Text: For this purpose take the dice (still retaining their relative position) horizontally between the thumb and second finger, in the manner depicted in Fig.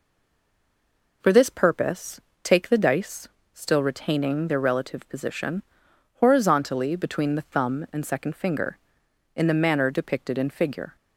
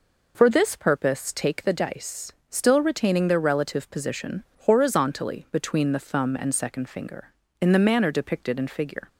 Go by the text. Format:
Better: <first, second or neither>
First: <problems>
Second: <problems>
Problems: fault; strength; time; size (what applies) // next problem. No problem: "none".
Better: second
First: stays silent before the first word; noticeable; until 1.2 s; 1.2 s long // pauses between "purpose" and "take"; slight; at 2.1 s; 0.22 s long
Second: none